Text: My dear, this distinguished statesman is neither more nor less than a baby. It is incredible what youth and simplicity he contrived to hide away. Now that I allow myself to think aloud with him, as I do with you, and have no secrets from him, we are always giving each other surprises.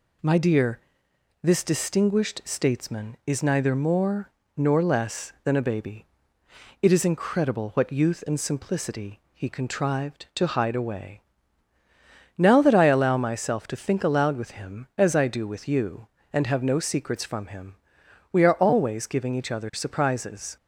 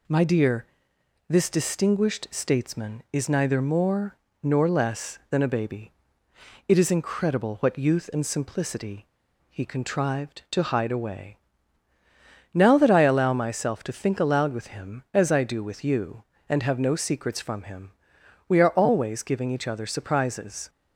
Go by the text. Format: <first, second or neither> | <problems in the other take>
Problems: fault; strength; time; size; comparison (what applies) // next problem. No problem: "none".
first | pauses between "more" and "nor"; slight; at 4.1 s; 0.26 s long; slight in the first // pauses between "simplicity" and "he"; at 9.0 s; 0.42 s long